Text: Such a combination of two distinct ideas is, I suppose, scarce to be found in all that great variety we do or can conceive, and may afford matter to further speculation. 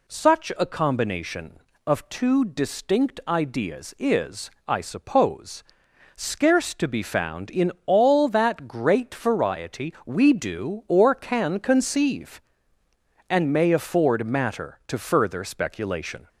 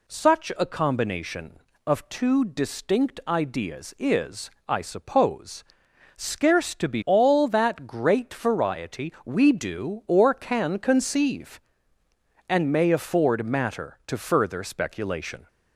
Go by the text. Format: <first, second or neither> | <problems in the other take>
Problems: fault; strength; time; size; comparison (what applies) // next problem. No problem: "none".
first | skips "found in"; at 7.0 s